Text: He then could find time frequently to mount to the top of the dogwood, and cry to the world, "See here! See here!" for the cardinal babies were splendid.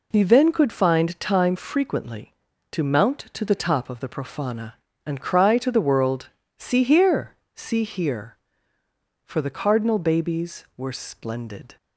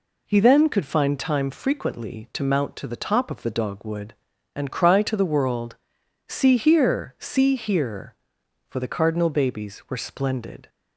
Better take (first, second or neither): second